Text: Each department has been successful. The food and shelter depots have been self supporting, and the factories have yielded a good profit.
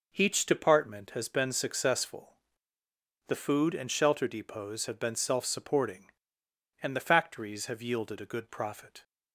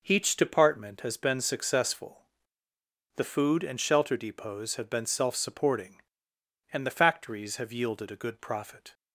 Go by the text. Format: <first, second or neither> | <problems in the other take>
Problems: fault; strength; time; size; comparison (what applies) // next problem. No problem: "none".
neither | none